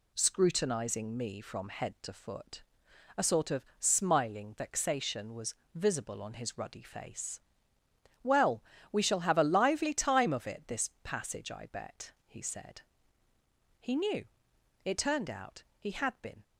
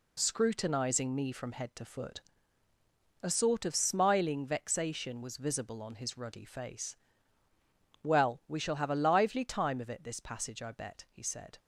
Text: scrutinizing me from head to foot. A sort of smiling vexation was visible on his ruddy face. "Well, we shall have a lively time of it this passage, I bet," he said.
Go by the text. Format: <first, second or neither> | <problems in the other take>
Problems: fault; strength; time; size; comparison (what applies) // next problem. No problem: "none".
second | pauses between "was" and "visible"; slight; at 5.5 s; 0.20 s long // goes on to say "He knew It turned out he had been"; strong; from 13.8 s on; 2.6 s long